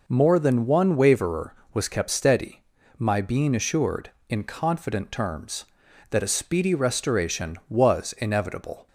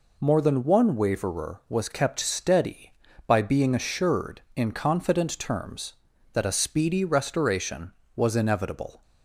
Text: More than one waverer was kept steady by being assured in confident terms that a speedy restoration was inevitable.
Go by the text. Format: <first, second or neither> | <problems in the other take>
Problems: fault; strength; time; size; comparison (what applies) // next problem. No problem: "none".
second | says "my" for "by"; at 2.9 s